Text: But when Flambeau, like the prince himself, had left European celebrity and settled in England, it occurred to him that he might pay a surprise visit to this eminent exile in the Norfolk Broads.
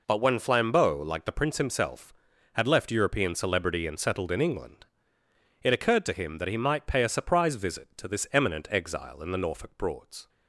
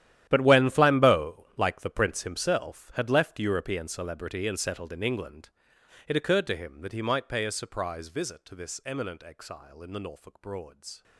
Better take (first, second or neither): first